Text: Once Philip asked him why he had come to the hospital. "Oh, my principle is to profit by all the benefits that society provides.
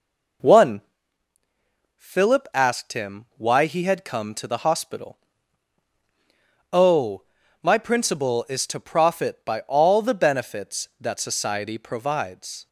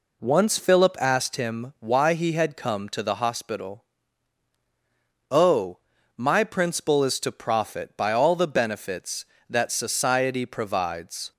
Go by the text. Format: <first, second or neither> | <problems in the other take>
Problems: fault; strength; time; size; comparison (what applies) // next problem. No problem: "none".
second | says "One" for "Once"; at 0.4 s